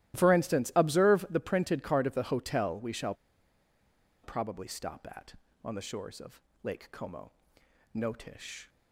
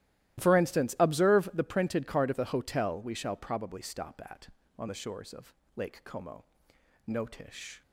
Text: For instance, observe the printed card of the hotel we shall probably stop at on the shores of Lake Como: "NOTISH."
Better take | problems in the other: second | starts louder than the rest; strong; until 1.1 s; 14.5 dB; strong in the second // pauses between "shall" and "probably"; at 3.1 s; 1.1 s long // pauses between "of" and "Lake"; slight; at 6.4 s; 0.24 s long; slight in the second

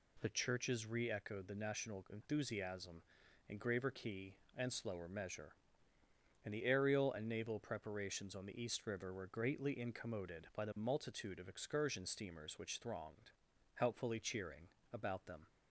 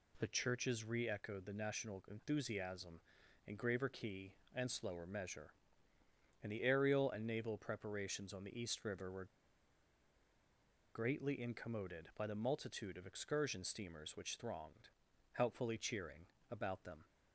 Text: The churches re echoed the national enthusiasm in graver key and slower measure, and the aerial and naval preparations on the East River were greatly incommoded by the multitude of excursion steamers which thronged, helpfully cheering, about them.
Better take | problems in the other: first | pauses between "were" and "greatly"; strong; at 9.2 s; 1.6 s long

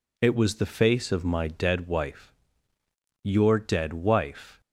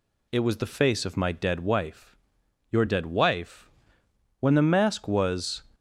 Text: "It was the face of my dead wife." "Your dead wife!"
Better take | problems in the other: first | goes on to say "When the mask was"; noticeable; from 4.4 s on; 1.2 s long

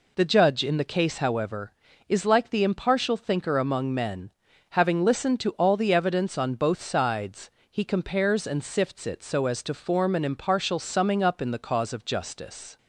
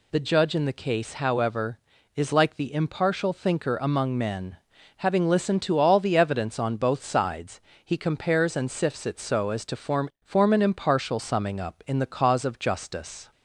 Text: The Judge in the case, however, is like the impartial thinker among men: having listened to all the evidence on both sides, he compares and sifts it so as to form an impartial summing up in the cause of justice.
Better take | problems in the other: first | says "form" twice; at 10.2 s

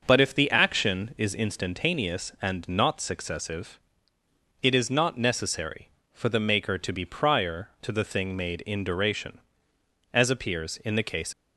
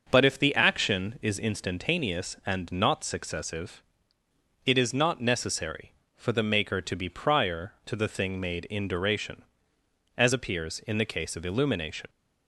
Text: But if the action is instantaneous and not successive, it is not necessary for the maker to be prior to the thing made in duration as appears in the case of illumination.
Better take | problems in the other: second | starts louder than the rest; until 1.0 s; 6.5 dB; also in the second // stops before "of illumination"; at 11.3 s

